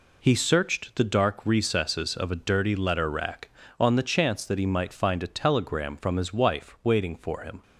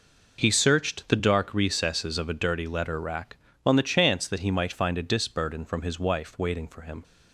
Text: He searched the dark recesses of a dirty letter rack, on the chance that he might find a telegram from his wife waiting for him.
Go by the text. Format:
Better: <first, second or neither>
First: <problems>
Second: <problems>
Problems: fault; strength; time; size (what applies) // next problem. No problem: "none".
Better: first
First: none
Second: says "disburden" for "telegram"; at 5.0 s